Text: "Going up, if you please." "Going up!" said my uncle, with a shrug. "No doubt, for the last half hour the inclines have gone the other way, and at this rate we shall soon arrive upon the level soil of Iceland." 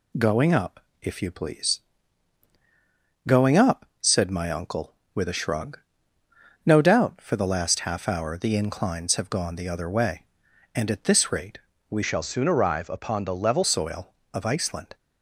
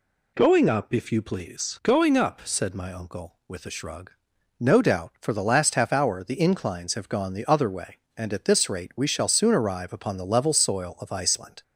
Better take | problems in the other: second | pauses between "rate" and "we"; slight; at 11.6 s; 0.28 s long // changes voice from "shall" to "level"; from 12.0 to 13.6 s; 1.6 s long

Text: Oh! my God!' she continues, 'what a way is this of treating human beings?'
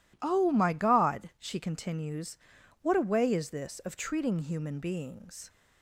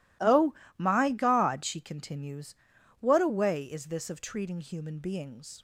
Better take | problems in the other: neither | none

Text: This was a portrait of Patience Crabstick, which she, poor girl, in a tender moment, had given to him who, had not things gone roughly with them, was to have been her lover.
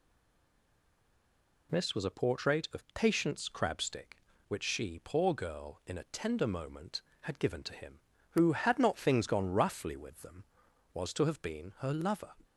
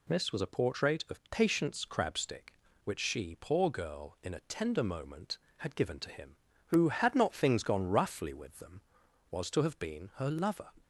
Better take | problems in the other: second | stays silent before the first word; noticeable; until 1.6 s; 1.6 s long

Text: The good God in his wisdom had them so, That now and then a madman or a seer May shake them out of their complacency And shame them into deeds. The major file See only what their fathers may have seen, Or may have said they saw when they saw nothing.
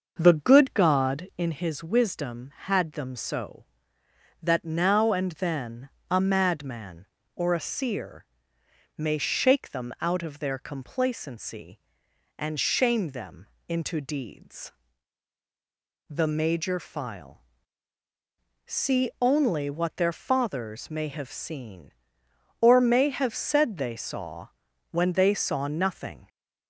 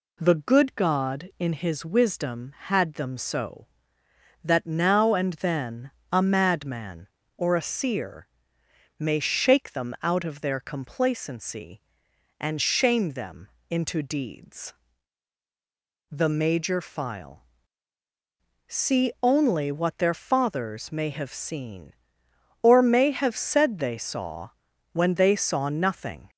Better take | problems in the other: second | starts louder than the rest; noticeable; until 1.5 s; 6 dB // pauses between "then" and "a"; slight; at 5.9 s; 0.20 s long; slight in the second // pauses between "seer" and "May"; noticeable; at 8.2 s; 0.72 s long; noticeable in the second // pauses between "them" and "into"; slight; at 13.4 s; 0.22 s long; slight in the second // pauses between "file" and "See"; at 17.4 s; 1.2 s long; also in the second // pauses between "saw" and "when"; at 24.4 s; 0.44 s long; also in the second

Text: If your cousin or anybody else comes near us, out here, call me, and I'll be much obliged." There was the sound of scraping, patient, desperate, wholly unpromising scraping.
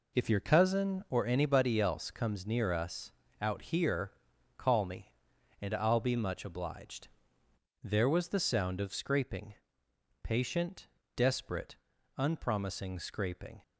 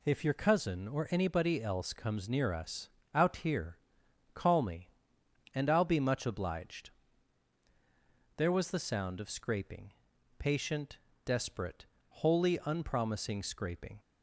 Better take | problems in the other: second | skips "wholly"; at 11.9 s

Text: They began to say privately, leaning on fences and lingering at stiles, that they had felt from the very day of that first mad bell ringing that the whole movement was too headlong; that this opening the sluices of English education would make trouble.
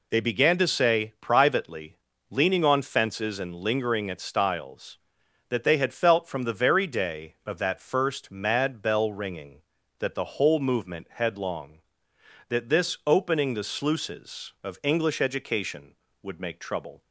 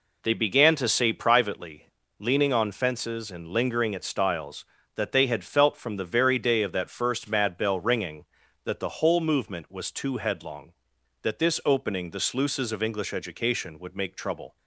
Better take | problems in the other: second | skips "was too"; at 11.1 s

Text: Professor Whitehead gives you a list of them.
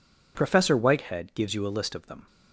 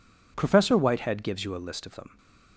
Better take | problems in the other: neither | none

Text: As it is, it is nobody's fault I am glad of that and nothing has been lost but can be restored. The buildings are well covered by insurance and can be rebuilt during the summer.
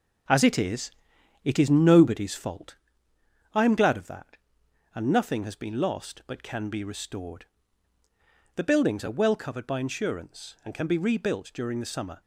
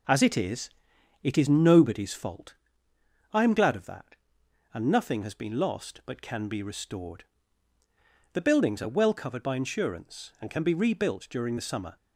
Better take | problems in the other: second | gets quieter; throughout; 6.5 dB // pauses between "fault" and "I"; noticeable; at 2.7 s; 0.78 s long; noticeable in the second

